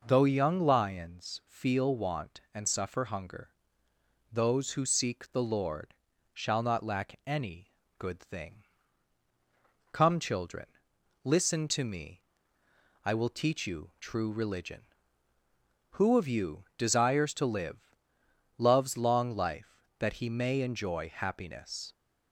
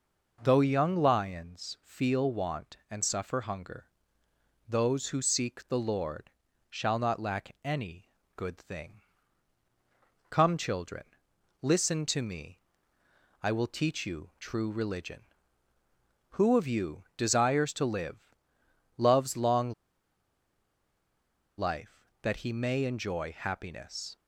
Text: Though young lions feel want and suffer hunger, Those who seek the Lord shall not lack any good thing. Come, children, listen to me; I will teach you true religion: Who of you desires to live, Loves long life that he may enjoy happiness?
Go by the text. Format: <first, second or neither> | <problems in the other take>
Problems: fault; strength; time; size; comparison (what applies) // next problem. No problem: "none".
first | pauses between "Lord" and "shall"; at 6.2 s; 0.40 s long; also in the first // pauses between "any" and "good"; slight; at 8.0 s; 0.32 s long; slight in the first // pauses between "long" and "life"; strong; at 19.7 s; 1.8 s long